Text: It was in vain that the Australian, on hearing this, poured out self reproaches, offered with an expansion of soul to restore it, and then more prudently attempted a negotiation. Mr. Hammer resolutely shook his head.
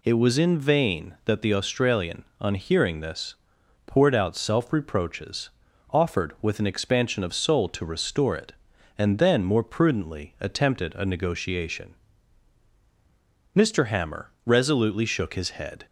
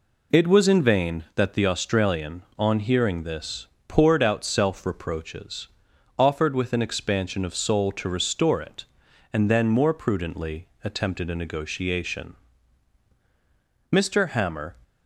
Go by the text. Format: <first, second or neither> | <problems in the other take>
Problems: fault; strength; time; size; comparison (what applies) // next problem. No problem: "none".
first | pauses between "prudently" and "attempted"; slight; at 10.6 s; 0.16 s long // stops before "resolutely shook his head"; at 14.8 s